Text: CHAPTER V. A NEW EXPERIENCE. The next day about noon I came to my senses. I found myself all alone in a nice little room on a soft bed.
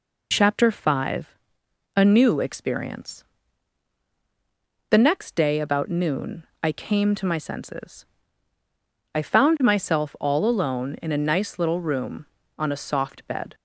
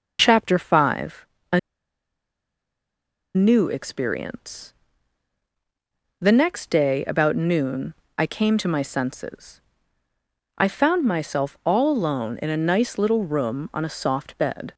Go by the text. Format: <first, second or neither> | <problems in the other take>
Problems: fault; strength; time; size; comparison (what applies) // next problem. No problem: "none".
first | pauses between "A" and "NEW"; strong; at 1.5 s; 1.7 s long // pauses between "noon" and "I"; slight; at 7.9 s; 0.24 s long; slight in the first